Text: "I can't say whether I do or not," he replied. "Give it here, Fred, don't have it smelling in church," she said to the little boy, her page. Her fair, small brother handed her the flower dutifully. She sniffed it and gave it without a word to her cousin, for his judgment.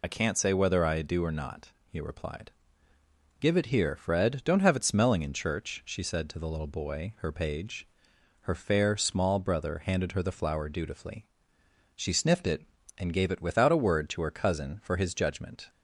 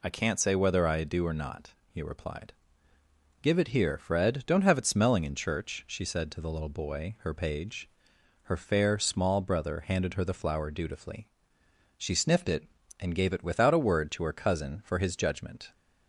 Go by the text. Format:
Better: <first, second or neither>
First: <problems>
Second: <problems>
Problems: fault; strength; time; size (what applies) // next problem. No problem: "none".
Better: second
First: loses the start of "I"; at 0.0 s; 25 ms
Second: none